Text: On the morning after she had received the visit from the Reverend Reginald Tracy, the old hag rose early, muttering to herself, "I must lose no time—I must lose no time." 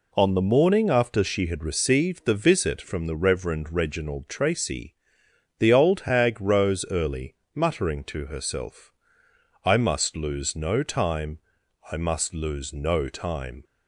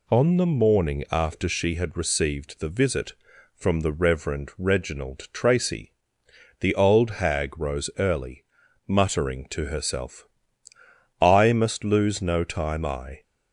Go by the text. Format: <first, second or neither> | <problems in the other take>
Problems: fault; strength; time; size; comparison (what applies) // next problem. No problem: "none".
first | stops before "must lose no time"; at 13.2 s